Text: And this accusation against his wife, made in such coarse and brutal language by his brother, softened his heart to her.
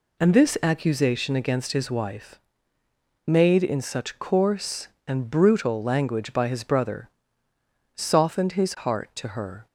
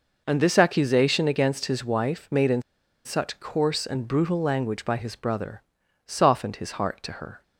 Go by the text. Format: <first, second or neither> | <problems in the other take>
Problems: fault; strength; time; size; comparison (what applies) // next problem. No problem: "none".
first | pauses between "in" and "such"; at 2.6 s; 0.43 s long